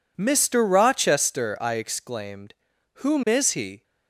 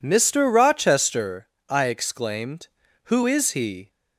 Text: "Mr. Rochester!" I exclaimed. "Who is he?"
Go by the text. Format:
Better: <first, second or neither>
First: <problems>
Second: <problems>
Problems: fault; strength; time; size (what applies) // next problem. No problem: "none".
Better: second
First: says "Whom" for "Who"; at 2.9 s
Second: none